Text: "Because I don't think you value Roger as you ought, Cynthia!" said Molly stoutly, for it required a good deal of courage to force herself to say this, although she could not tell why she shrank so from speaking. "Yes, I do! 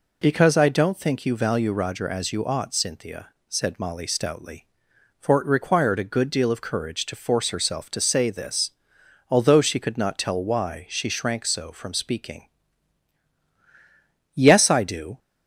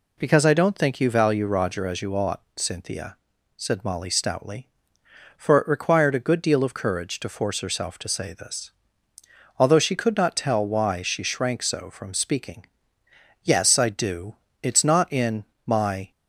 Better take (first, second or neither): first